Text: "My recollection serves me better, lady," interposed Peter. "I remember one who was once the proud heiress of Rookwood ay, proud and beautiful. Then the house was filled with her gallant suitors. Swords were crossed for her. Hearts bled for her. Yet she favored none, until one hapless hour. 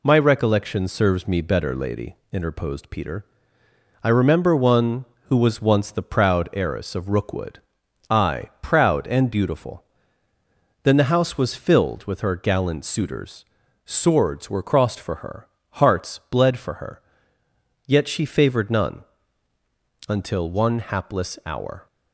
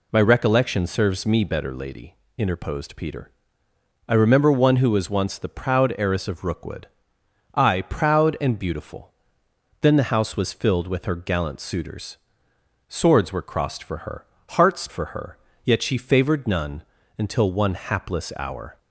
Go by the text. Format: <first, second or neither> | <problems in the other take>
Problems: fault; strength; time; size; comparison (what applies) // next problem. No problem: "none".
first | pauses between "Rookwood" and "ay"; noticeable; at 6.8 s; 0.66 s long; noticeable in the first // skips "bled"; at 14.8 s